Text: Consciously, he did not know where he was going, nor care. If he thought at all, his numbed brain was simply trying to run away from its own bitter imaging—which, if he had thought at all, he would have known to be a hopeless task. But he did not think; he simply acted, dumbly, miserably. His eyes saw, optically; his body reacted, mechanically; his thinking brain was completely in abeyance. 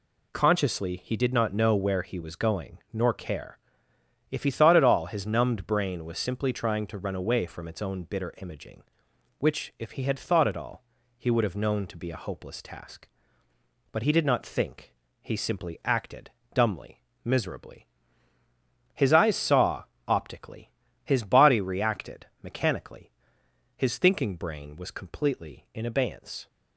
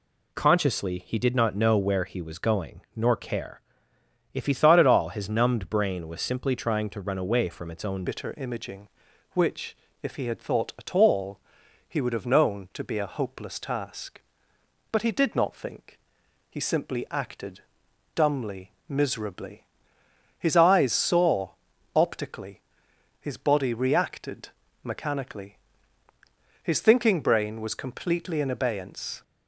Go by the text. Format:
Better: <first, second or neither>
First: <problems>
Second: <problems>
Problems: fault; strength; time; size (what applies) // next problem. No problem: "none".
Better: first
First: none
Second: changes voice at "bitter"; from 8.0 s on; 21.2 s long